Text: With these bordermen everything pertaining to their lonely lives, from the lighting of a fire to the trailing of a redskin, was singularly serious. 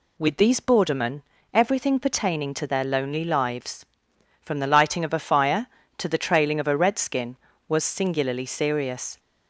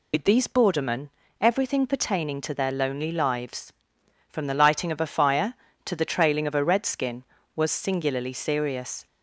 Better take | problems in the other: first | loses the start of "With"; at 0.1 s; 75 ms // pauses between "bordermen" and "everything"; slight; at 1.0 s; 0.32 s long; slight in the first

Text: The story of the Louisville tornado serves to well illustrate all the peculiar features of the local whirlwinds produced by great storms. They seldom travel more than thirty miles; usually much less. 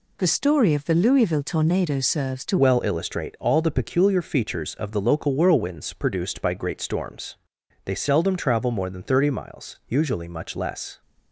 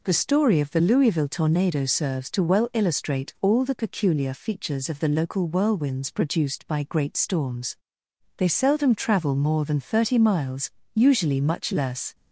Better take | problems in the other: second | changes voice at "well"; from 2.5 s on; 8.5 s long

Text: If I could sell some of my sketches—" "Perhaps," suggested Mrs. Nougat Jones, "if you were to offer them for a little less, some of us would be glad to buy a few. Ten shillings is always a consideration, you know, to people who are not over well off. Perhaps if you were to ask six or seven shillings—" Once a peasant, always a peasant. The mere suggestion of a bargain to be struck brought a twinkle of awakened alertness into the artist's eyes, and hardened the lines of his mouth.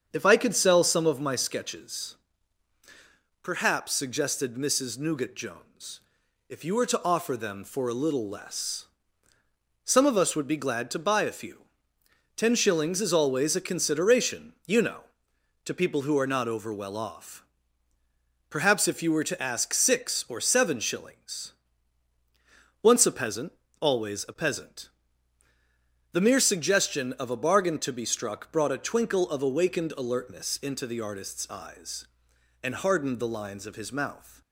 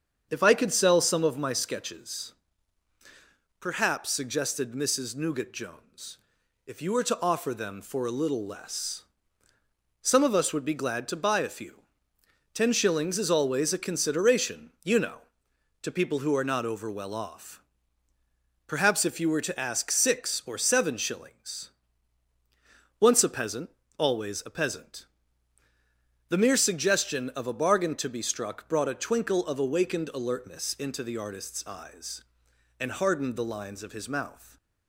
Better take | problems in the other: neither | starts louder than the rest; strong; the same in both

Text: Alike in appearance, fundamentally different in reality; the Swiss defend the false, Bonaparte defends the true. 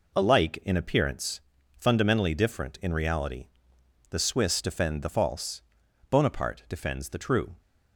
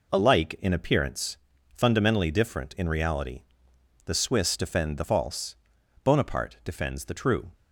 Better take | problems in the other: neither | none

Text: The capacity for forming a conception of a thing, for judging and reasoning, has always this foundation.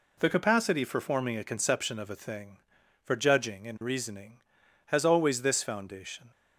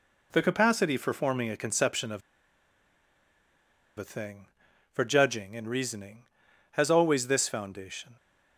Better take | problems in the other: first | pauses between "of" and "a"; strong; at 2.2 s; 1.7 s long

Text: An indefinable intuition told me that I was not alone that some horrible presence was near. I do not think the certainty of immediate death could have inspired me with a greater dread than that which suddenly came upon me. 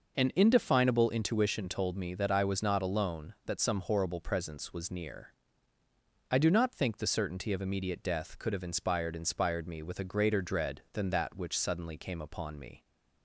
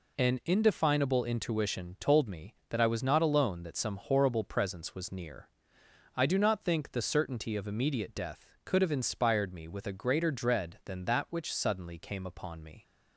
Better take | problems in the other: second | says "inspired" twice; at 9.1 s

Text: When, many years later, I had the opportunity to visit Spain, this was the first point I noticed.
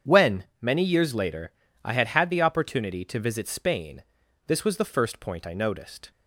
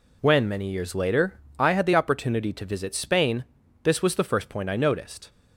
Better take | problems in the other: second | starts louder than the rest; strong; until 1.2 s; 8 dB // says "had" twice; at 2.0 s

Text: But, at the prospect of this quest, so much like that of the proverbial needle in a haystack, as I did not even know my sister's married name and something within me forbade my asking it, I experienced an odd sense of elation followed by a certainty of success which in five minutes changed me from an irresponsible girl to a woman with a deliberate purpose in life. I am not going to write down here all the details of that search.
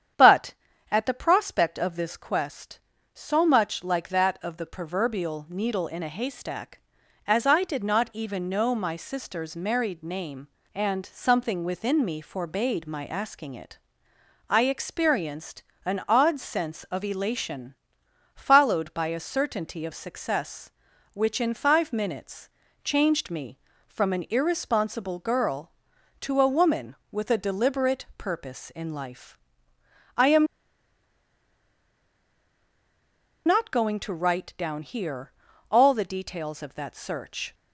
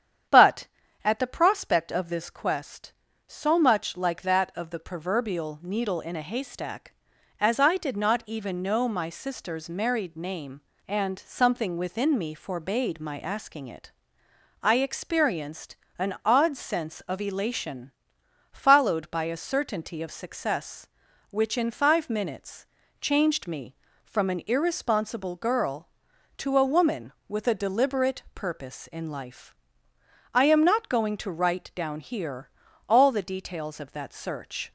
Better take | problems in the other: second | starts louder than the rest; strong; until 1.5 s; 9 dB; strong in the second // pauses between "experienced" and "an"; slight; at 15.6 s; 0.22 s long; slight in the second // pauses between "elation" and "followed"; noticeable; at 17.7 s; 0.60 s long; noticeable in the second // pauses between "minutes" and "changed"; slight; at 22.4 s; 0.34 s long; slight in the second // pauses between "am" and "not"; strong; at 30.4 s; 2.9 s long // pauses between "here" and "all"; at 35.3 s; 0.38 s long; also in the second

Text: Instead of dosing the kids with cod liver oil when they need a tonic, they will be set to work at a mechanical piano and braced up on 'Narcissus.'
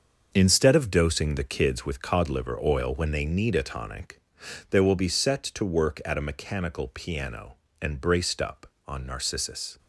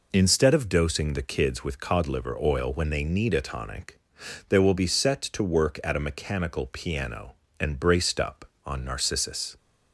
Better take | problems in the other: second | gets quieter; strong; throughout; 8.5 dB

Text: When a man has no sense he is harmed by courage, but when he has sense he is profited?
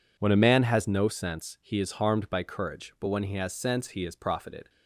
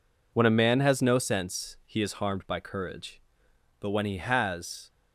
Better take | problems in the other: first | stops before "sense he is profited"; at 4.8 s

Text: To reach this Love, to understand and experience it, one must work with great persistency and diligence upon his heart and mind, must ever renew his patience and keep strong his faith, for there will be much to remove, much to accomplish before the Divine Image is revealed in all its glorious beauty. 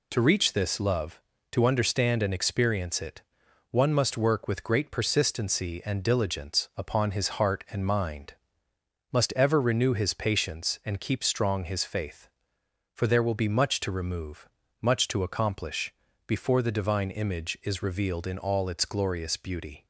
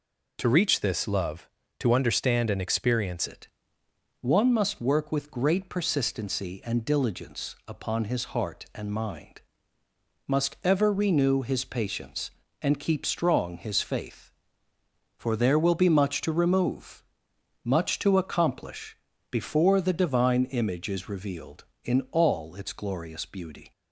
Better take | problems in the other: first | changes voice at "it"; from 3.2 s on; 20.5 s long // pauses between "accomplish" and "before"; slight; at 18.9 s; 0.34 s long; slight in the first

